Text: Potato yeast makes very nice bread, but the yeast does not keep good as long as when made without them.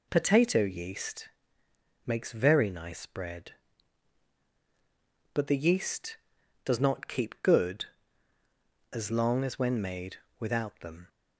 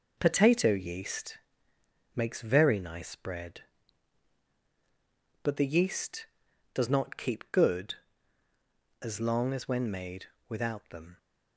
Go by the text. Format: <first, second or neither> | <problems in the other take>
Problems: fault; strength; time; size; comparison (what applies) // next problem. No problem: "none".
first | gets quieter; throughout; 6.5 dB // pauses between "yeast" and "makes"; noticeable; at 1.3 s; 0.78 s long; noticeable in the first // pauses between "made" and "without"; slight; at 10.2 s; 0.24 s long; slight in the first